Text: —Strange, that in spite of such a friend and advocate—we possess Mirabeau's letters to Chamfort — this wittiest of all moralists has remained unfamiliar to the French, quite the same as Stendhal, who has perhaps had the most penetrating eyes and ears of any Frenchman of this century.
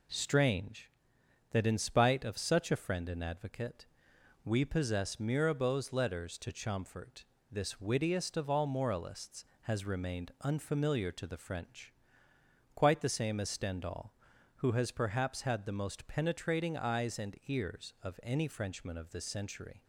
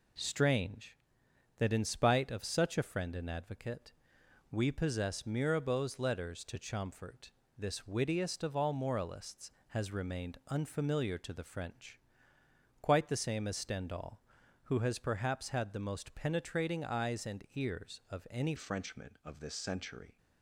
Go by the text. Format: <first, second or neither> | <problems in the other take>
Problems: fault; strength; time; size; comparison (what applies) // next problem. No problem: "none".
first | changes voice at "Frenchman"; from 18.5 s on; 1.6 s long